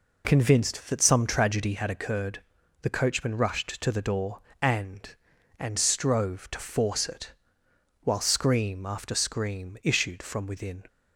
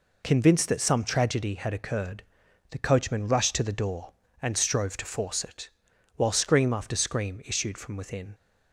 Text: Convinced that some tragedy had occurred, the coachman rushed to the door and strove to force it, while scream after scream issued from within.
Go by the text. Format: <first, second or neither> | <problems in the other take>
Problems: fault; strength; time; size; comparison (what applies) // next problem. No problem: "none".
second | says "and" twice; at 5.5 s